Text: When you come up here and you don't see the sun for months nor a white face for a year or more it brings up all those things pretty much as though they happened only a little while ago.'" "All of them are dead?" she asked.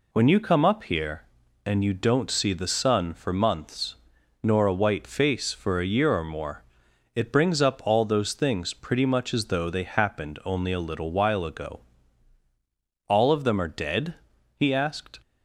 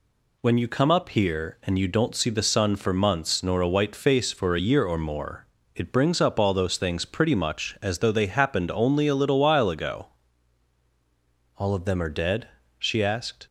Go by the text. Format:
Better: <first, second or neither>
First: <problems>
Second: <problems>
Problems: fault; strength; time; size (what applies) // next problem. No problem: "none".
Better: second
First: pauses between "months" and "nor"; noticeable; at 3.9 s; 0.48 s long // pauses between "more" and "it"; noticeable; at 6.6 s; 0.50 s long // says "he" for "she"; at 14.5 s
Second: pauses between "more" and "it"; slight; at 5.4 s; 0.28 s long